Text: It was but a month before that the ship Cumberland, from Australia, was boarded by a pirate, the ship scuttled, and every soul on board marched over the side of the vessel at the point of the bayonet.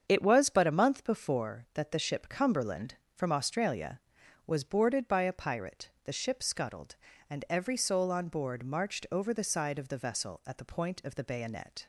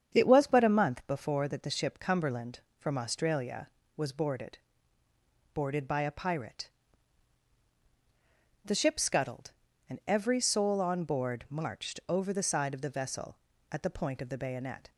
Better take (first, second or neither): first